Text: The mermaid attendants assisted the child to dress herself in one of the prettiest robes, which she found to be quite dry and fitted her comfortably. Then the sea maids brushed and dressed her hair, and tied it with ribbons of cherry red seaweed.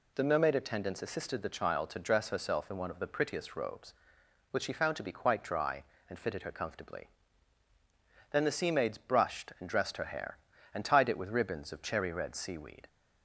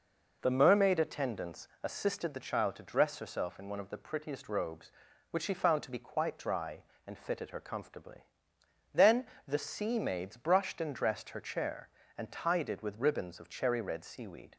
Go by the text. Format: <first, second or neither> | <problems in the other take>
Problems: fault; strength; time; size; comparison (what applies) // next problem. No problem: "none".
first | pauses between "attendants" and "assisted"; slight; at 1.6 s; 0.16 s long // pauses between "Then" and "the"; slight; at 9.2 s; 0.20 s long // says "chair" for "hair"; at 11.4 s